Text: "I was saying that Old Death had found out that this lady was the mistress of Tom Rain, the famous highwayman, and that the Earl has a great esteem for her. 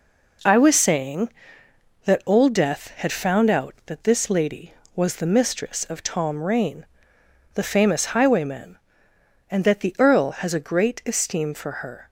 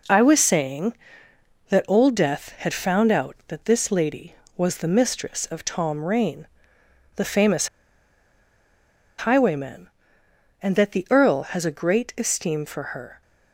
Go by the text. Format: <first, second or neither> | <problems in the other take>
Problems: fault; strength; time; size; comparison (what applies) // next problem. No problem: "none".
first | pauses between "famous" and "highwayman"; strong; at 7.6 s; 1.5 s long // pauses between "for" and "her"; slight; at 12.8 s; 0.16 s long; slight in the first